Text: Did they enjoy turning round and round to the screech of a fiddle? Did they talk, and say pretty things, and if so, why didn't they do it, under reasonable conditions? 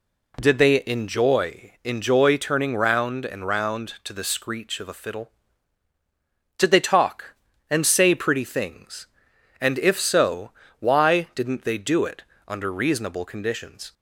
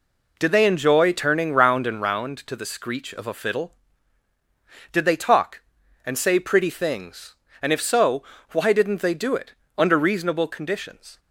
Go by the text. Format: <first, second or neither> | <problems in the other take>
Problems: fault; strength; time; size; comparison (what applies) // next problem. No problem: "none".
second | says "enjoy" twice; at 1.8 s